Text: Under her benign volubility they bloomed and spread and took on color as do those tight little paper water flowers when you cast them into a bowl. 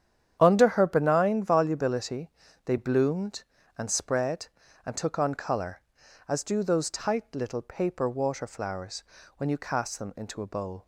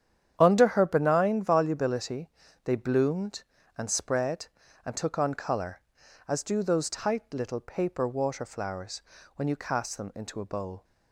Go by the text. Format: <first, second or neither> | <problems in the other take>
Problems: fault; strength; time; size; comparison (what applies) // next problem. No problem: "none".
neither | starts louder than the rest; strong; the same in both // pauses between "volubility" and "they"; slight; the same in both // pauses between "flowers" and "when"; slight; the same in both